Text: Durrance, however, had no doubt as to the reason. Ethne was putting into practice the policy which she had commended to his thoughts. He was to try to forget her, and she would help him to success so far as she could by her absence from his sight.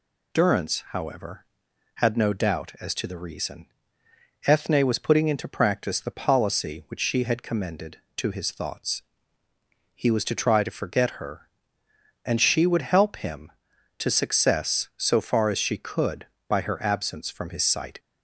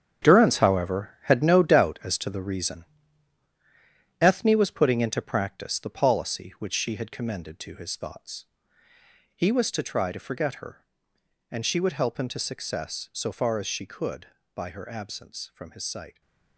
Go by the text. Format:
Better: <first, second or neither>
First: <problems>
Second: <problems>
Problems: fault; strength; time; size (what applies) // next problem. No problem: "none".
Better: first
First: none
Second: gets quieter; strong; throughout; 11.5 dB